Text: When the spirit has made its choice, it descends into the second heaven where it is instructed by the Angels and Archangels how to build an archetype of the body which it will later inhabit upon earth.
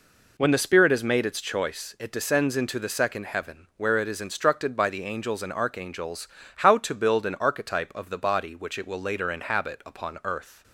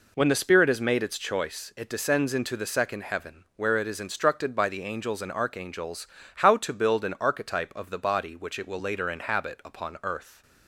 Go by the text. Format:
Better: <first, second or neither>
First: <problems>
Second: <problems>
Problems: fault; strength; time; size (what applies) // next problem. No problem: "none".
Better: neither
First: pauses between "Archangels" and "how"; slight; at 6.2 s; 0.28 s long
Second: pauses between "Archangels" and "how"; slight; at 6.0 s; 0.28 s long